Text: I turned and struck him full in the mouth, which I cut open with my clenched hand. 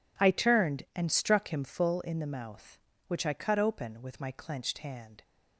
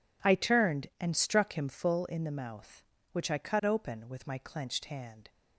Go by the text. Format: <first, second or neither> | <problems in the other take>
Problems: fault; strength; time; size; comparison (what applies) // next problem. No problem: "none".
neither | none